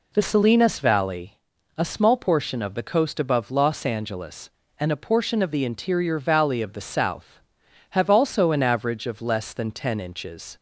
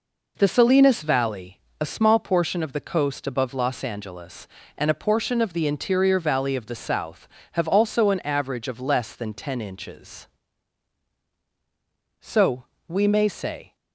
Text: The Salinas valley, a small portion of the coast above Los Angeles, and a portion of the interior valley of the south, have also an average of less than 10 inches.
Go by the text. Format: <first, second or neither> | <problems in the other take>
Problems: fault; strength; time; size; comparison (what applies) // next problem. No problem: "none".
first | goes on to say "So we may say"; from 12.2 s on; 1.5 s long